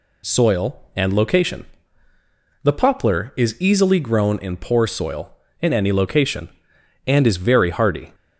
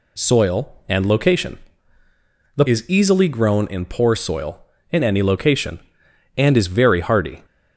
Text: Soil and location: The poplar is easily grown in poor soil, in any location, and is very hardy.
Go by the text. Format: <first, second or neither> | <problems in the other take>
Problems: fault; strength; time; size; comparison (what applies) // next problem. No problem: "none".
first | skips "poplar"; at 2.6 s